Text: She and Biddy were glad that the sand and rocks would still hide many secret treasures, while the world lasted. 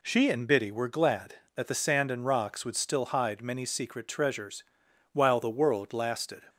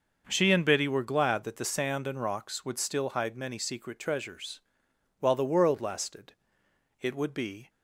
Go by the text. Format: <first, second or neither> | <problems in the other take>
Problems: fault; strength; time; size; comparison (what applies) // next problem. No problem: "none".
first | starts louder than the rest; noticeable; until 1.2 s; 6 dB // goes on to say "It would be"; noticeable; from 6.9 s on; 0.70 s long